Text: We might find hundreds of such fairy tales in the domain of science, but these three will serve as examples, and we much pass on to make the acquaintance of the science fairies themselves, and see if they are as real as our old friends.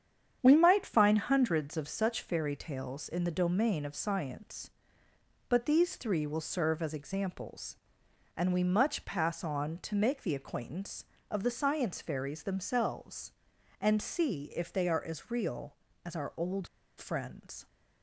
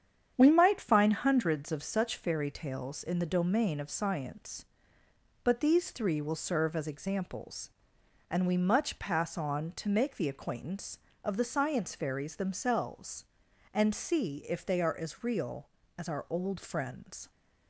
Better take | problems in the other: second | starts louder than the rest; strong; until 1.4 s; 8.5 dB; strong in the second // pauses between "old" and "friends"; slight; at 16.6 s; 0.30 s long

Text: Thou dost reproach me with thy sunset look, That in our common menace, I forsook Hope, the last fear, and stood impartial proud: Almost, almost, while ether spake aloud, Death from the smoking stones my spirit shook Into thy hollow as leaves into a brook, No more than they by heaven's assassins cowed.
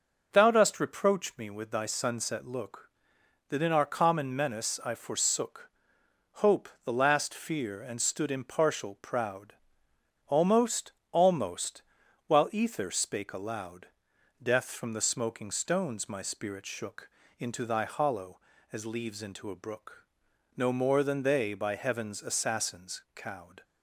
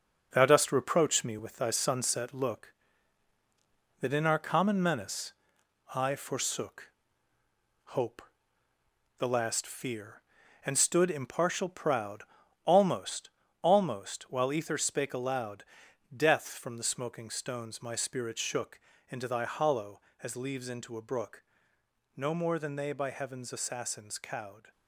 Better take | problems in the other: first | gets quieter; throughout; 6.5 dB // pauses between "forsook" and "Hope"; noticeable; at 6.9 s; 0.94 s long; noticeable in the first // pauses between "shook" and "Into"; slight; at 18.7 s; 0.30 s long; slight in the first

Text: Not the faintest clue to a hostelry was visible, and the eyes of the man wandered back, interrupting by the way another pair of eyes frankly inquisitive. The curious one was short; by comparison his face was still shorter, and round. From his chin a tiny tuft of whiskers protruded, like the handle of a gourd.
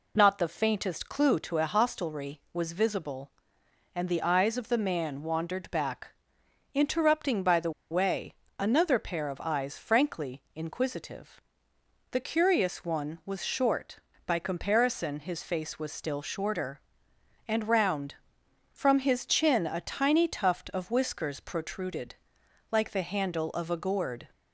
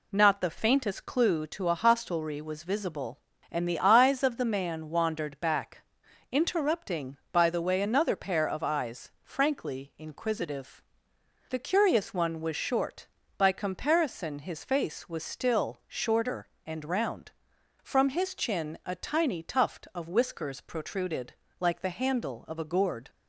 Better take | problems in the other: second | pauses between "the" and "way"; slight; at 7.7 s; 0.20 s long // pauses between "way" and "another"; slight; at 8.3 s; 0.24 s long

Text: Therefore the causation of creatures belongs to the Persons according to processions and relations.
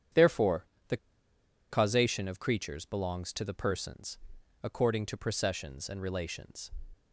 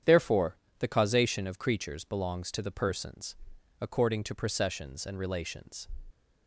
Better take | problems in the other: second | starts louder than the rest; strong; until 2.0 s; 9 dB; strong in the second // pauses between "Therefore" and "the"; slight; at 0.6 s; 0.22 s long; slight in the second // pauses between "the" and "causation"; noticeable; at 0.9 s; 0.73 s long // pauses between "Persons" and "according"; at 4.1 s; 0.44 s long; also in the second

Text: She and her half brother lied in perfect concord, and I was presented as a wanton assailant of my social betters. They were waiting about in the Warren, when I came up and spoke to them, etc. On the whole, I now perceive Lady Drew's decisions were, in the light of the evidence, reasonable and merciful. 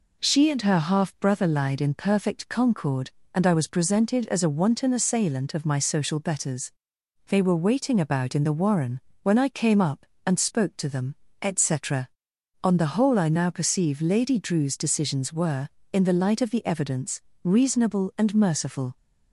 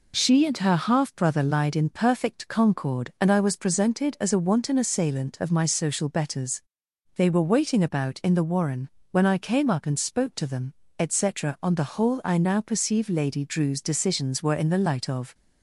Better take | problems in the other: first | stops before "the evidence reasonable and merciful"; at 15.3 s

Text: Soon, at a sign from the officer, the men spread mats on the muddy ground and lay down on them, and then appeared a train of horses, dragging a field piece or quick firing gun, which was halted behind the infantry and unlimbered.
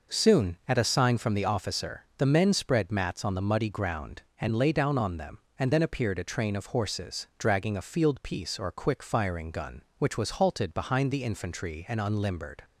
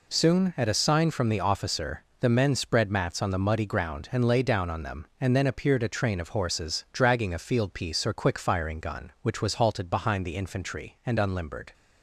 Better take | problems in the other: neither | none

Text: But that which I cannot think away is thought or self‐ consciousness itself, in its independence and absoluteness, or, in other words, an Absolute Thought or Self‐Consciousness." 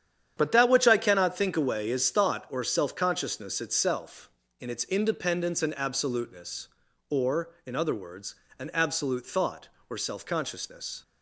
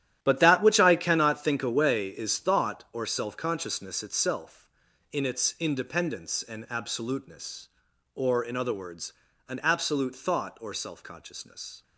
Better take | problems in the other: first | gets quieter; strong; throughout; 12 dB // starts louder than the rest; strong; until 1.2 s; 11.5 dB; strong in the first

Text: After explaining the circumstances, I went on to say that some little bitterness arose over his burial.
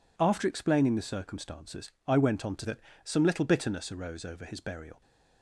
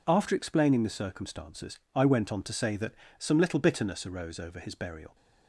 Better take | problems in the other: second | skips "say"; at 2.6 s // pauses between "that" and "some"; slight; at 2.7 s; 0.26 s long; slight in the second

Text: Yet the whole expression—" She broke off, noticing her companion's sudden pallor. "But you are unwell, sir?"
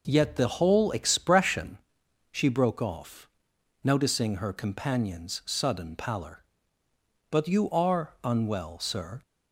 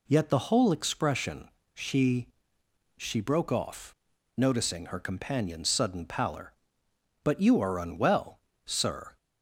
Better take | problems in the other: first | says "She" twice; at 2.9 s

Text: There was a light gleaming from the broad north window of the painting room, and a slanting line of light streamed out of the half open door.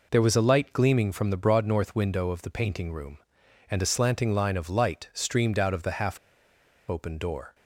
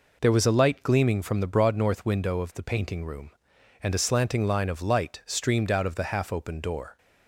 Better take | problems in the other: second | pauses between "half" and "open"; noticeable; at 6.1 s; 0.72 s long

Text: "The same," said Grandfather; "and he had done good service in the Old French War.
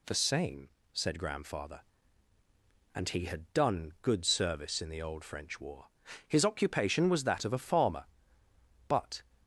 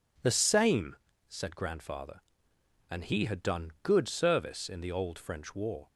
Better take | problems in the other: second | goes on to say "His occupation was that of a farmer but"; strong; from 6.2 s on; 2.9 s long

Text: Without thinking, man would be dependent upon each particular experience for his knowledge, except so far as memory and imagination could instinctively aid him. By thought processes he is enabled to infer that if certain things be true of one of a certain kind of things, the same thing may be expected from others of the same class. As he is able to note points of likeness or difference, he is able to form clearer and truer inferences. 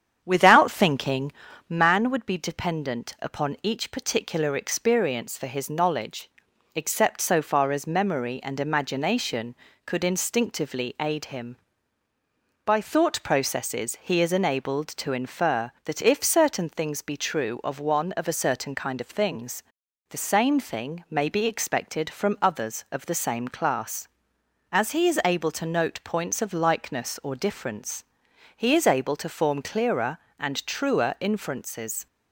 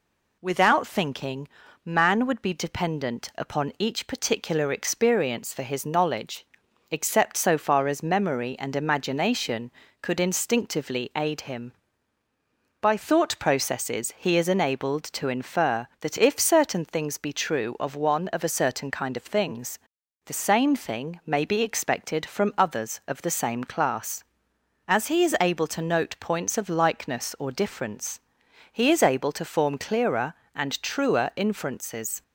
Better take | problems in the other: second | starts louder than the rest; strong; until 2.0 s; 8.5 dB

